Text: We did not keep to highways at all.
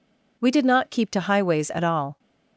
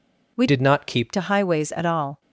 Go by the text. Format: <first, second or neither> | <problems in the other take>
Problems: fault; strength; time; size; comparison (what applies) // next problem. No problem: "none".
first | changes voice from "did" to "keep"; from 0.4 to 1.1 s; 0.7 s long